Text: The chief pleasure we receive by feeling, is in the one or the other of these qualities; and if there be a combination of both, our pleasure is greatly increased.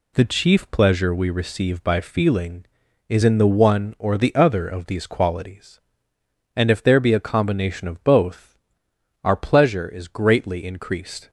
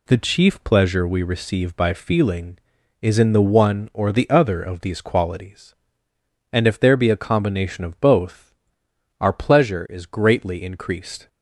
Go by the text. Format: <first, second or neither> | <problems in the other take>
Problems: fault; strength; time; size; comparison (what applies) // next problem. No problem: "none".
neither | none